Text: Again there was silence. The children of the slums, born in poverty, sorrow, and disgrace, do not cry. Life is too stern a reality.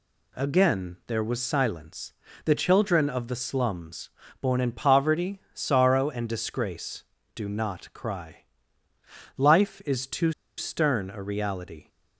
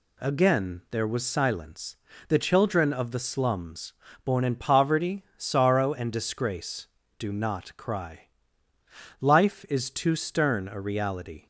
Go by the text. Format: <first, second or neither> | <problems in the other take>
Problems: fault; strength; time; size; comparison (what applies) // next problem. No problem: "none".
second | pauses between "too" and "stern"; slight; at 10.3 s; 0.25 s long